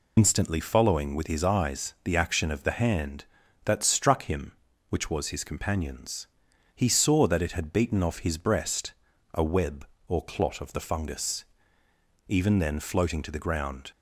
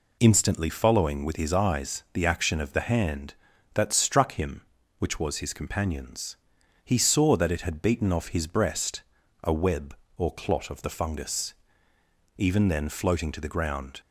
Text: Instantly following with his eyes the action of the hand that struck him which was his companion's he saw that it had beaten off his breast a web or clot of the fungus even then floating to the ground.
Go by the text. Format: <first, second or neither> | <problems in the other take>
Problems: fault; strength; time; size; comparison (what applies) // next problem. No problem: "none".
second | loses the start of "Instantly"; at 0.1 s; 65 ms // pauses between "companion's" and "he"; noticeable; at 6.2 s; 0.48 s long; noticeable in the second // pauses between "breast" and "a"; at 8.9 s; 0.42 s long; also in the second // pauses between "fungus" and "even"; noticeable; at 11.4 s; 0.82 s long; noticeable in the second